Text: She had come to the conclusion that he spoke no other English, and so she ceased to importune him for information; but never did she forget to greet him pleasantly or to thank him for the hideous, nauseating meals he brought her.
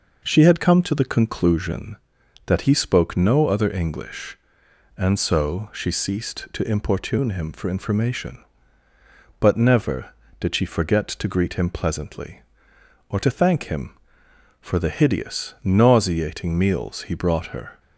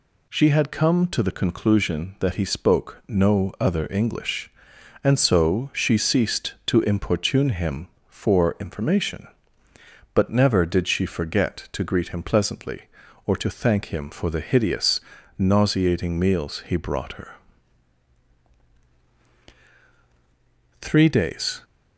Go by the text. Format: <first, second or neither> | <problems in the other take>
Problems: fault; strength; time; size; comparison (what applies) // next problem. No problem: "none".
first | goes on to say "Three days"; noticeable; from 20.8 s on; 0.80 s long